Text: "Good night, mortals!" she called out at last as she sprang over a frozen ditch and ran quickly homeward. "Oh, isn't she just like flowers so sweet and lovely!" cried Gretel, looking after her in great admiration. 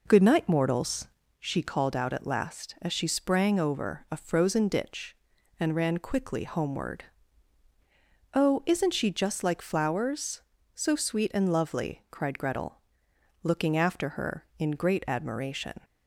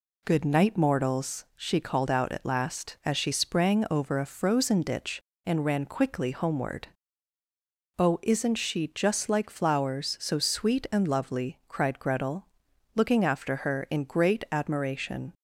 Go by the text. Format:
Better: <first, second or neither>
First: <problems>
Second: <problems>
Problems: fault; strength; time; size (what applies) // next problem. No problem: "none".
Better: second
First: starts louder than the rest; noticeable; until 1.4 s; 4.5 dB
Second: none